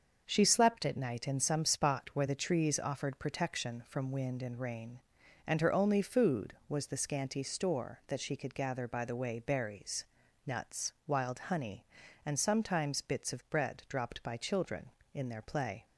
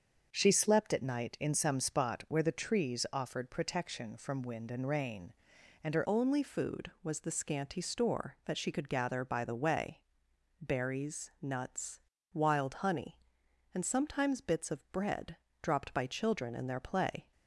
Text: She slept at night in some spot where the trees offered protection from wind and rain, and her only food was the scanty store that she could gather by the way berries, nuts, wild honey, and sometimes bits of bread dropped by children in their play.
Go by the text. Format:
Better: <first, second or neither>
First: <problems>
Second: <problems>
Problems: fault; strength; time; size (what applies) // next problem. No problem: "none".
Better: first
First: starts louder than the rest; until 1.2 s; 6.5 dB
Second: starts louder than the rest; until 1.3 s; 6.5 dB // changes voice at "only"; from 6.0 s on; 11.3 s long // pauses between "way" and "berries"; noticeable; at 10.0 s; 0.58 s long // pauses between "bread" and "dropped"; slight; at 15.3 s; 0.26 s long